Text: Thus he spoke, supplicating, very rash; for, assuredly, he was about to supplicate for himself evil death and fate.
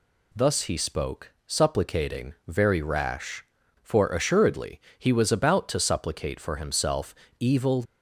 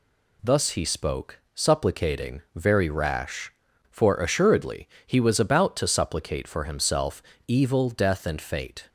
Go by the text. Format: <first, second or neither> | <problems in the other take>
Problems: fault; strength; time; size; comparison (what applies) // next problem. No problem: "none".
second | pauses between "himself" and "evil"; slight; at 7.1 s; 0.24 s long; slight in the second // stops before "death and fate"; at 7.8 s